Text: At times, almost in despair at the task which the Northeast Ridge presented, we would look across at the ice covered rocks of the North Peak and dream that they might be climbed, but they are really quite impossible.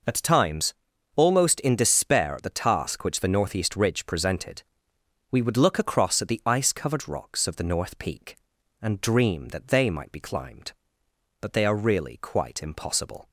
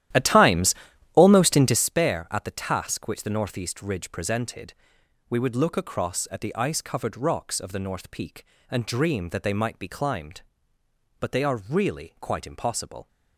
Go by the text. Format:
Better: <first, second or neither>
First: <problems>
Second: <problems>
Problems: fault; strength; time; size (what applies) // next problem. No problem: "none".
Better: first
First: none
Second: starts louder than the rest; strong; until 2.0 s; 13 dB